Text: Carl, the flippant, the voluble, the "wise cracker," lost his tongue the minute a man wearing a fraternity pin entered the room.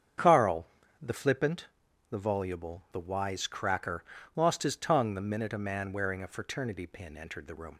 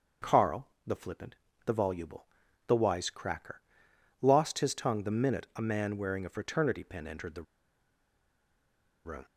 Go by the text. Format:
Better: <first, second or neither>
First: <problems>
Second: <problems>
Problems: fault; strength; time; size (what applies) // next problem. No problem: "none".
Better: first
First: starts louder than the rest; strong; until 1.5 s; 7.5 dB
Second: starts louder than the rest; until 1.7 s; 6.5 dB // pauses between "the" and "room"; strong; at 7.4 s; 1.6 s long